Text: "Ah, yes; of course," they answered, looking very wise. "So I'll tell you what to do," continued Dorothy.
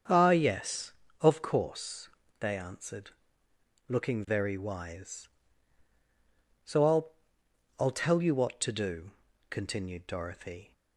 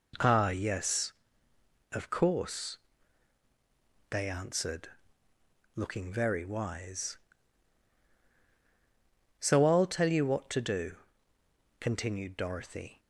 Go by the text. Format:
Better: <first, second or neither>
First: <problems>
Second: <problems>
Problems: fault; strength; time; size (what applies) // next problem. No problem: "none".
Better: second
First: starts louder than the rest; strong; until 1.3 s; 7.5 dB // says "I'll" twice; at 7.7 s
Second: none